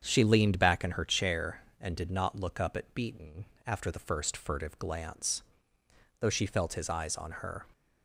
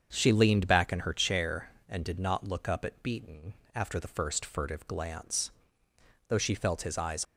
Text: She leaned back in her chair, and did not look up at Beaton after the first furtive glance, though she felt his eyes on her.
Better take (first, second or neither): first